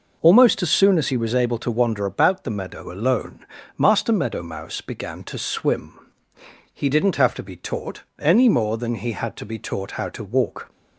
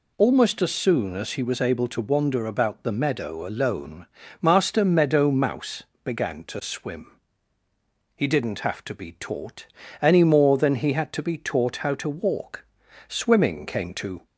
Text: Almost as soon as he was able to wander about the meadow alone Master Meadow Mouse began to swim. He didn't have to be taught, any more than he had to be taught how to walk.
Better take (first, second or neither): first